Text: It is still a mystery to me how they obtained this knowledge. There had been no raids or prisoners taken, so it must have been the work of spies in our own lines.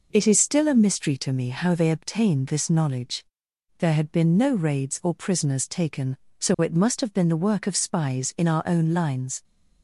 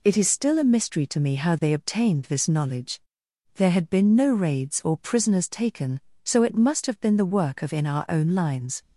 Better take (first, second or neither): first